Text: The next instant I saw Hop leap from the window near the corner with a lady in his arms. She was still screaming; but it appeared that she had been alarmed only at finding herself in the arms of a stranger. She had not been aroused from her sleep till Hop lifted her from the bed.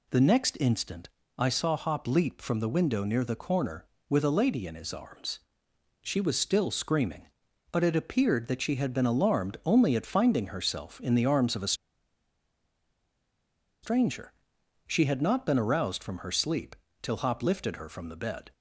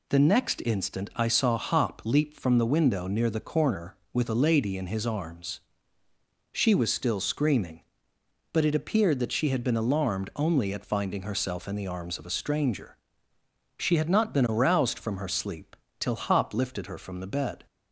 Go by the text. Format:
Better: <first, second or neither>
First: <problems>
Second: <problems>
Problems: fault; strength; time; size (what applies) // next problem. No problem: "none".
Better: second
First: pauses between "instant" and "I"; slight; at 1.0 s; 0.28 s long // pauses between "a" and "stranger"; strong; at 11.7 s; 2.0 s long // pauses between "sleep" and "till"; slight; at 16.7 s; 0.26 s long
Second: pauses between "sleep" and "till"; slight; at 15.7 s; 0.24 s long